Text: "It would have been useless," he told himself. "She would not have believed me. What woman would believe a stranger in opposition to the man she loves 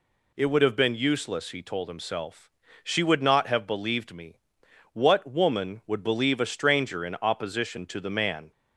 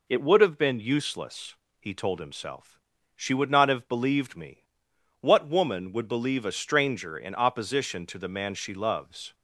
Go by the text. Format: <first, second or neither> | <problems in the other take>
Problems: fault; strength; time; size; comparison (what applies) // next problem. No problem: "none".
second | stops before "she loves"; at 8.5 s